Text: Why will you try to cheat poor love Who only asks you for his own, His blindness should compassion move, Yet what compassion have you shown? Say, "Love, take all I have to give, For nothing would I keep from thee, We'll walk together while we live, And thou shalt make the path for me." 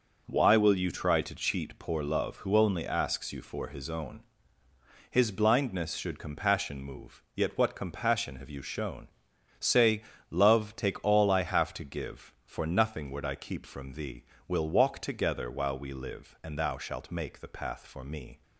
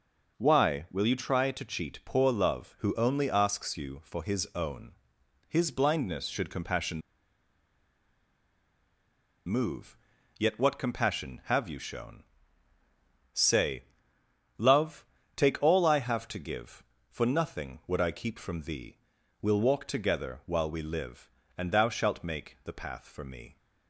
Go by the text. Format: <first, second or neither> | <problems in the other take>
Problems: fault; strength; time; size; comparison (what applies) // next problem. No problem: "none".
first | pauses between "compassion" and "move"; strong; at 7.0 s; 2.4 s long